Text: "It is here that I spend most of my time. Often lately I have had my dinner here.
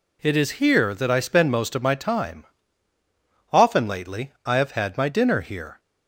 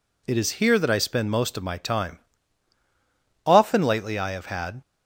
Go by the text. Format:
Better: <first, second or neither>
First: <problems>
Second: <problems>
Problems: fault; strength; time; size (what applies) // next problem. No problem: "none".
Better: first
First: none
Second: stops before "my dinner here"; at 4.8 s